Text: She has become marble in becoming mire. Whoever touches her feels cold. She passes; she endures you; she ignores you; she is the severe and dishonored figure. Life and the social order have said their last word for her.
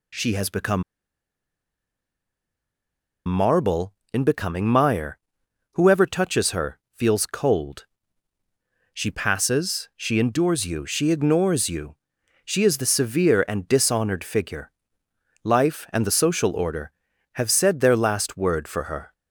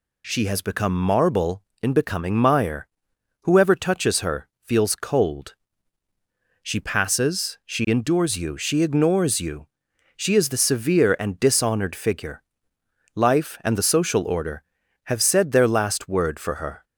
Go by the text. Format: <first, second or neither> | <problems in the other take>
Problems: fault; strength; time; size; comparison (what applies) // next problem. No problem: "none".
second | pauses between "become" and "marble"; strong; at 0.8 s; 2.4 s long // pauses between "her" and "feels"; slight; at 6.7 s; 0.16 s long; slight in the second